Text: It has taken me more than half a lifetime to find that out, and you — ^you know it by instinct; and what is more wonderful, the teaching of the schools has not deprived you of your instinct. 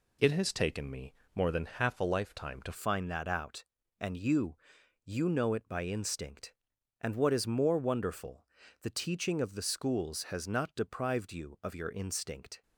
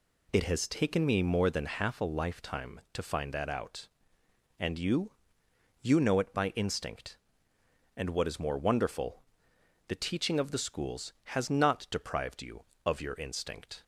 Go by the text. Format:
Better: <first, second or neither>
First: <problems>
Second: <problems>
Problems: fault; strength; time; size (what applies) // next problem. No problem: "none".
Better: second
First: pauses between "me" and "more"; slight; at 1.1 s; 0.20 s long // changes voice at "find"; from 2.7 s on; 9.9 s long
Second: none